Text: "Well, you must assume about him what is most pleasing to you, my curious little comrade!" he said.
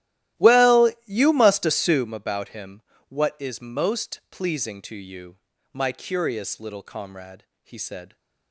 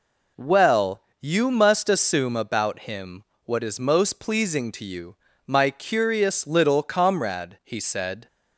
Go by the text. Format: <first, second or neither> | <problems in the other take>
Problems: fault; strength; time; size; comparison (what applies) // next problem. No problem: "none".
second | starts louder than the rest; strong; until 2.1 s; 14.5 dB // pauses between "him" and "what"; slight; at 2.8 s; 0.26 s long; slight in the second